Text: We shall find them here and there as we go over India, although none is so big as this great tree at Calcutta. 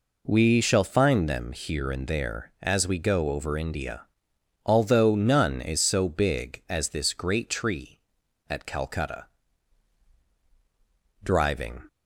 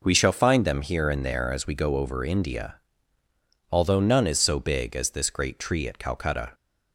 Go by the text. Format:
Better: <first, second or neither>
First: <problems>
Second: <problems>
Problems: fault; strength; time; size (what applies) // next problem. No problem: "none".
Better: second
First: goes on to say "Driving"; noticeable; from 11.2 s on; 0.64 s long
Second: none